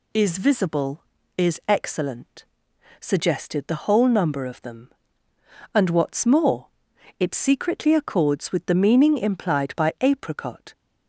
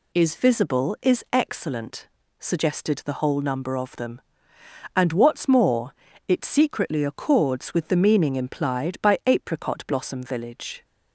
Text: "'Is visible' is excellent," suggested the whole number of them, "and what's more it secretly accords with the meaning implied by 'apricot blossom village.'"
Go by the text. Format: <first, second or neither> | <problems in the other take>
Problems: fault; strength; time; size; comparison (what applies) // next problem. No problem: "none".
second | pauses between "more" and "it"; noticeable; at 6.6 s; 0.50 s long; slight in the second // stops before "blossom village"; at 10.7 s